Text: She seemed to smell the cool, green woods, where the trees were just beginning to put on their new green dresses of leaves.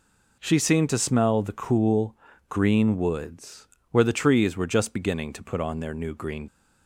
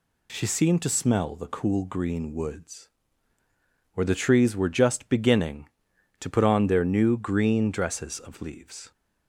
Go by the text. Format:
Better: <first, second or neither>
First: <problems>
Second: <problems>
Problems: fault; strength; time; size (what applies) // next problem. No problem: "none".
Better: second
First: stops before "dresses of leaves"; at 6.4 s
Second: none